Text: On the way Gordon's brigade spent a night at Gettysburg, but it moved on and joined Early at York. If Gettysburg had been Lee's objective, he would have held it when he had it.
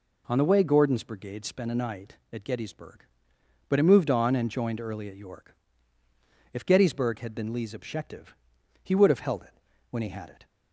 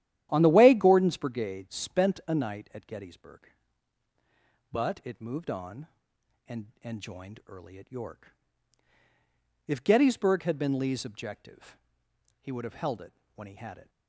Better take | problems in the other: first | starts louder than the rest; strong; until 1.3 s; 11.5 dB // says "and" twice; at 6.8 s // pauses between "it" and "when"; slight; at 13.1 s; 0.22 s long; slight in the first

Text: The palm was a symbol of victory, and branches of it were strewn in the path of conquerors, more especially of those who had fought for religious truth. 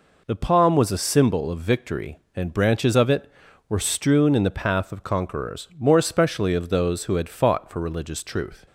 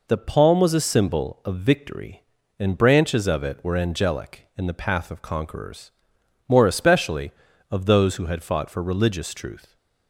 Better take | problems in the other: first | says "angelic" for "strewn"; at 3.7 s

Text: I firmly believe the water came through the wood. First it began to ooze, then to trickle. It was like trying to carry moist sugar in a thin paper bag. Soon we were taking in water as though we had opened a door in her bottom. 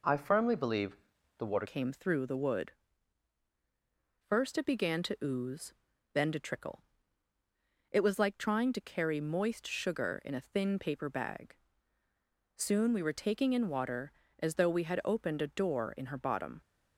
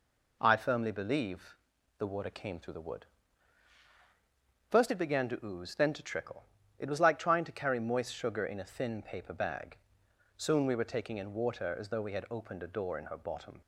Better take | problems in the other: second | pauses between "believe" and "the"; at 0.9 s; 0.42 s long; also in the second // changes voice at "came"; from 1.6 s on; 15.0 s long

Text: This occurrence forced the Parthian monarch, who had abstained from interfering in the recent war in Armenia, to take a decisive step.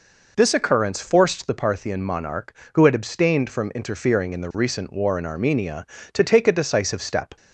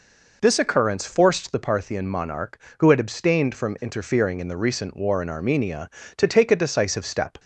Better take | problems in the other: neither | none

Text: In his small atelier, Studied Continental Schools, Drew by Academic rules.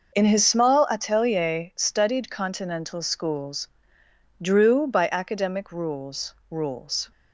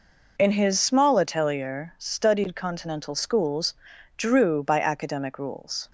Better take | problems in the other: second | says "rules" twice; at 6.4 s

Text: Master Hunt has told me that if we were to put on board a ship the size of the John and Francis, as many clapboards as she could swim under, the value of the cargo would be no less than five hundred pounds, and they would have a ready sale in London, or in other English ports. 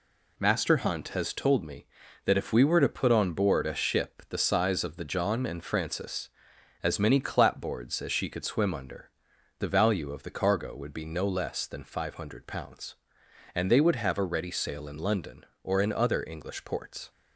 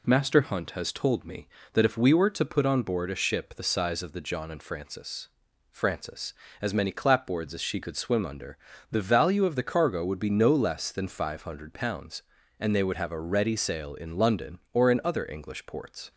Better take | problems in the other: first | says "Francis" twice; at 5.7 s

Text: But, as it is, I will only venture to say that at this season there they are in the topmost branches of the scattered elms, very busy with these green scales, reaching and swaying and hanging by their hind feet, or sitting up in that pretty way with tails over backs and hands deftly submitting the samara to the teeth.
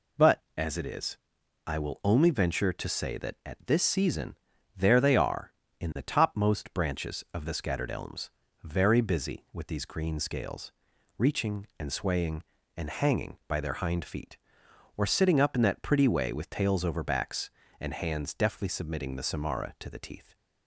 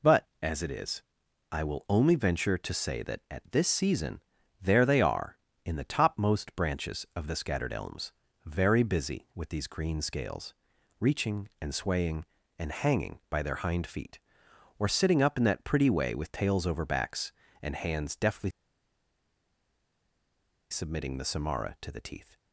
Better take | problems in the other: first | pauses between "season" and "there"; at 4.2 s; 0.42 s long; also in the first // pauses between "deftly" and "submitting"; strong; at 18.5 s; 2.2 s long

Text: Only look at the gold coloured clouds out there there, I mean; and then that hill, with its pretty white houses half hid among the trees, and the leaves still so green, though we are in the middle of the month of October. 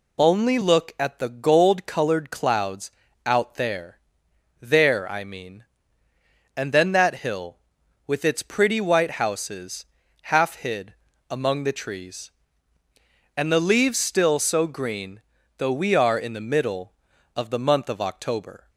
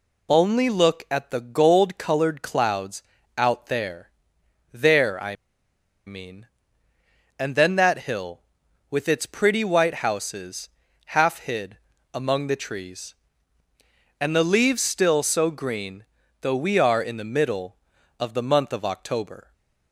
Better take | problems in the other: first | pauses between "clouds" and "out"; slight; at 3.0 s; 0.34 s long; slight in the first // pauses between "there" and "there"; noticeable; at 4.0 s; 0.62 s long; noticeable in the first // pauses between "I" and "mean"; noticeable; at 5.3 s; 0.72 s long // pauses between "houses" and "half"; noticeable; at 10.6 s; 0.48 s long; noticeable in the first // pauses between "hid" and "among"; slight; at 11.7 s; 0.34 s long; slight in the first

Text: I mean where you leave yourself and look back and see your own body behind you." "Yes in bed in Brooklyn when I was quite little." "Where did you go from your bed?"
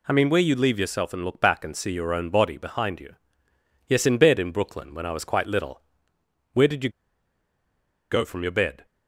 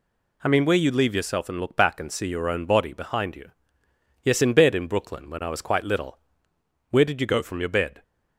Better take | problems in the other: second | pauses between "you" and "go"; at 6.8 s; 1.2 s long

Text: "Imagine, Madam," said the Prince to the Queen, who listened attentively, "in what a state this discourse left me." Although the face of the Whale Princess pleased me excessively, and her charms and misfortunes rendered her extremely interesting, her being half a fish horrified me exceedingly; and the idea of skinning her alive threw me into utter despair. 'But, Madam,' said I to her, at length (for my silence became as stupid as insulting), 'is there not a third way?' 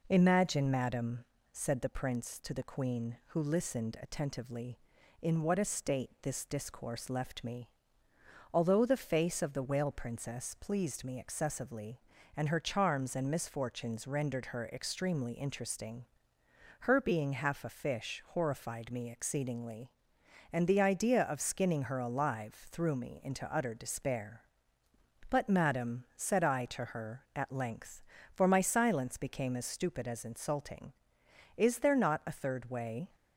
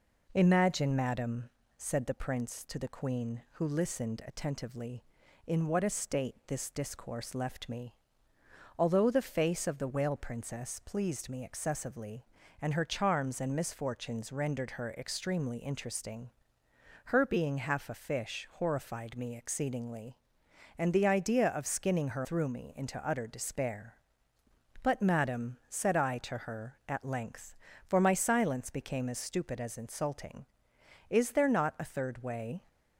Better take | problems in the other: first | skips "alive"; at 22.2 s

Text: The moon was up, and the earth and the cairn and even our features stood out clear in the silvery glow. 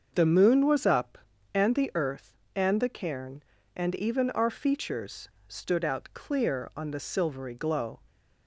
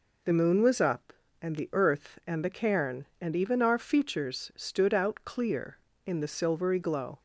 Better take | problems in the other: second | starts louder than the rest; until 1.1 s; 6.5 dB // pauses between "features" and "stood"; slight; at 5.2 s; 0.19 s long // says "on" for "in"; at 6.7 s

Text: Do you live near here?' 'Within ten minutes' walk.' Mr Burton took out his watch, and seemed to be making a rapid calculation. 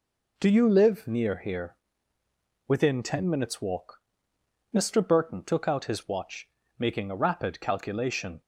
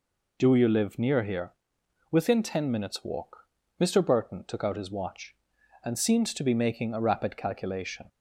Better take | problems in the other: second | skips "and seemed to be"; at 6.6 s

